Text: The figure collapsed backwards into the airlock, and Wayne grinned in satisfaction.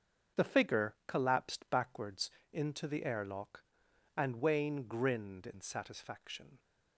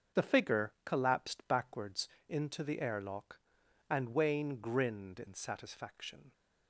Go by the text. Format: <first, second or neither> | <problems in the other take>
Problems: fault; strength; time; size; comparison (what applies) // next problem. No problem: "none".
neither | starts louder than the rest; strong; the same in both // pauses between "backwards" and "into"; slight; the same in both